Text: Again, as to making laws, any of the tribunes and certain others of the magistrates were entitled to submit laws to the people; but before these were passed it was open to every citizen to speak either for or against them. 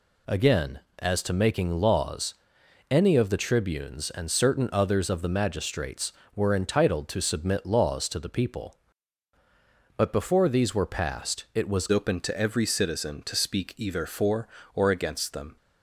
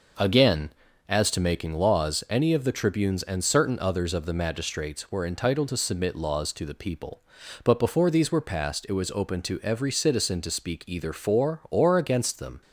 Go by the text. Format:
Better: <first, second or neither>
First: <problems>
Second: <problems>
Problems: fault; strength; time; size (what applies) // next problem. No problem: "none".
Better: second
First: changes voice at "open"; from 11.8 s on; 3.7 s long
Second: none